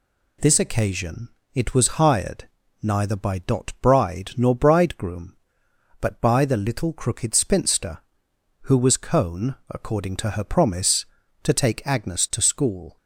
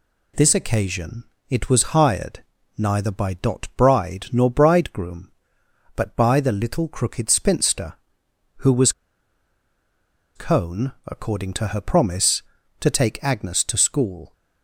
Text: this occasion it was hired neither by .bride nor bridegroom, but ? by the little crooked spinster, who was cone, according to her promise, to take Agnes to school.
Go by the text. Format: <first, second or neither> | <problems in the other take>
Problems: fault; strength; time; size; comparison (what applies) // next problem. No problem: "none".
first | pauses between "occasion" and "it"; slight; at 1.2 s; 0.26 s long; slight in the first // pauses between "hired" and "neither"; slight; at 2.4 s; 0.34 s long; slight in the first // pauses between "was" and "cone"; strong; at 8.9 s; 1.4 s long